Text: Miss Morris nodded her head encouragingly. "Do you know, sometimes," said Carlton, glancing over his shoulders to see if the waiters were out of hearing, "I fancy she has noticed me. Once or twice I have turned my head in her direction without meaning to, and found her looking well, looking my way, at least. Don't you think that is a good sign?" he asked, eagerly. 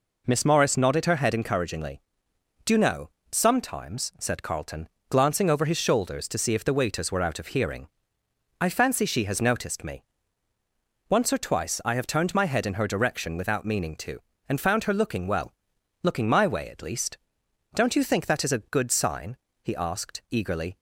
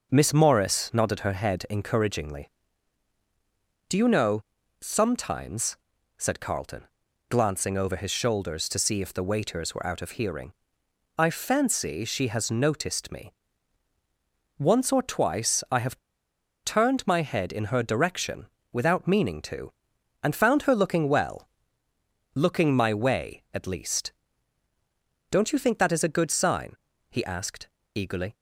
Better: first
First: none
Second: pauses between "have" and "turned"; noticeable; at 15.9 s; 0.65 s long // pauses between "direction" and "without"; slight; at 18.4 s; 0.24 s long

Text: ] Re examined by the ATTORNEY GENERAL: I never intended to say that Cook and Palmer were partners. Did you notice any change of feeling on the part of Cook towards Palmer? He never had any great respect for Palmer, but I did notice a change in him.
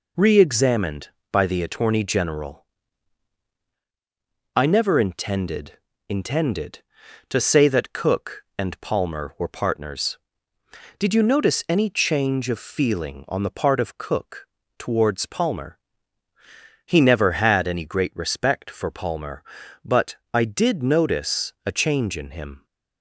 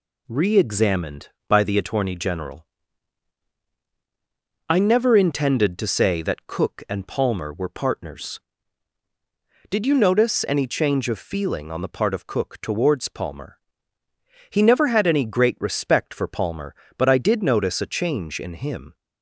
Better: second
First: says "intended" twice; at 6.0 s // pauses between "Cook" and "towards"; slight; at 14.4 s; 0.30 s long // pauses between "but" and "I"; slight; at 20.1 s; 0.16 s long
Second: none

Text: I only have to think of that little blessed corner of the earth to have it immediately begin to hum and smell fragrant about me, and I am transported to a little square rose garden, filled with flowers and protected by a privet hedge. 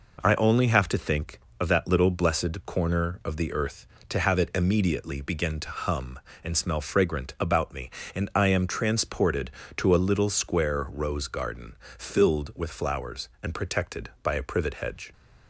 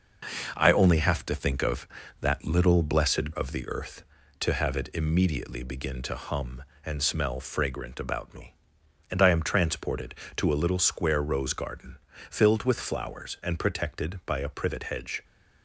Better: first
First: none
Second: skips "corner"; at 3.3 s

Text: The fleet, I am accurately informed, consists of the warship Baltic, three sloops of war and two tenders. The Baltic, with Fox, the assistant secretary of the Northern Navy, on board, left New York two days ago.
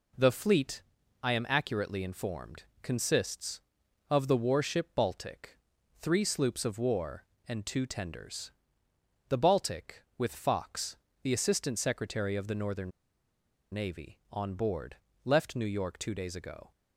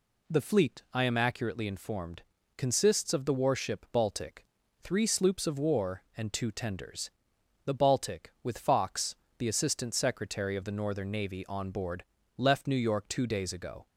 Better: second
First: pauses between "Northern" and "Navy"; noticeable; at 12.9 s; 0.81 s long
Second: none

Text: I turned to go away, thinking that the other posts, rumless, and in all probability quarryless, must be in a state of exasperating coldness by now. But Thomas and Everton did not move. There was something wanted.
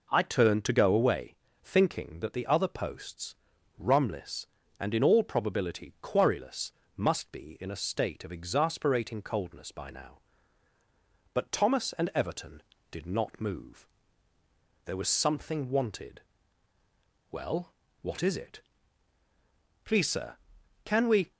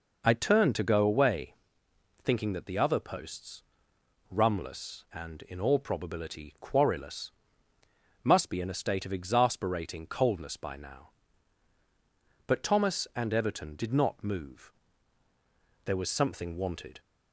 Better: second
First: goes on to say "Well what is it Please sir can we"; strong; from 17.3 s on; 4.0 s long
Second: none

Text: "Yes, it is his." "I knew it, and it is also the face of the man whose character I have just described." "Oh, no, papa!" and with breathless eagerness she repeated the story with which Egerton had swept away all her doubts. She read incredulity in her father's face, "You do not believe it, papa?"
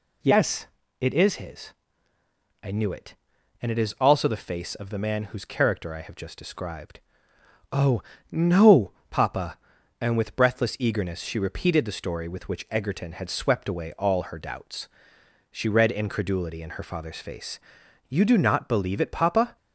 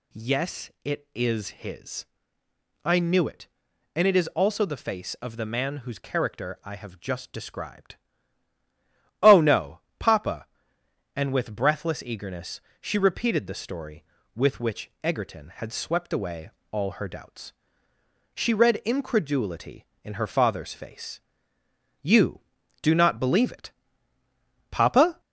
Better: first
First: none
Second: gets louder; slight; throughout; 2.5 dB // pauses between "eagerness" and "she"; slight; at 12.5 s; 0.22 s long // pauses between "away" and "all"; slight; at 16.4 s; 0.22 s long

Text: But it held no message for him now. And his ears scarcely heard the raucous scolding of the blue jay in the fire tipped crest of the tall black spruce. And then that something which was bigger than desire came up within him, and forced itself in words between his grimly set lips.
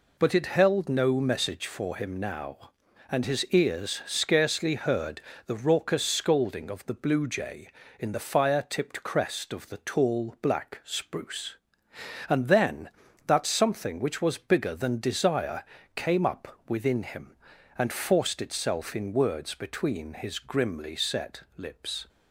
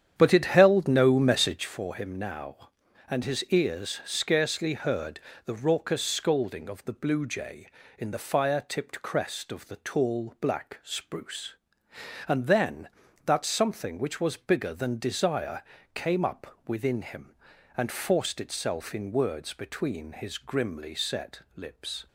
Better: first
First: pauses between "heard" and "the"; slight; at 5.2 s; 0.26 s long // pauses between "desire" and "came"; slight; at 15.6 s; 0.30 s long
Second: starts louder than the rest; strong; until 1.8 s; 9 dB // pauses between "heard" and "the"; slight; at 5.1 s; 0.26 s long // pauses between "desire" and "came"; slight; at 15.6 s; 0.30 s long

